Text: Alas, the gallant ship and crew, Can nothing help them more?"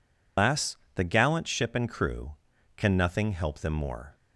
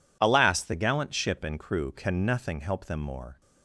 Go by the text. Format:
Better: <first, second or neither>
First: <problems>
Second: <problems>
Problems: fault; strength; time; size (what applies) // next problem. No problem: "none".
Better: second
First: loses the start of "Alas"; at 0.3 s; 165 ms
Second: none